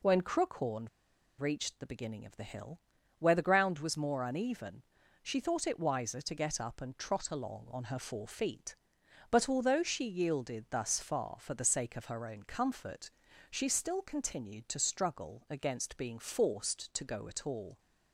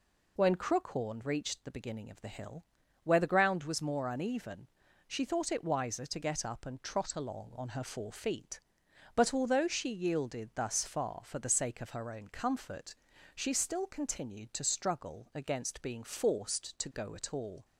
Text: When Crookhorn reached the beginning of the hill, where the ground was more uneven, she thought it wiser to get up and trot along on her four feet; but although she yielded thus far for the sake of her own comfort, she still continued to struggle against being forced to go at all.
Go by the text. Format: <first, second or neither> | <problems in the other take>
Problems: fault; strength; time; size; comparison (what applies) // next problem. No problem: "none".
second | pauses between "Crookhorn" and "reached"; noticeable; at 0.8 s; 0.50 s long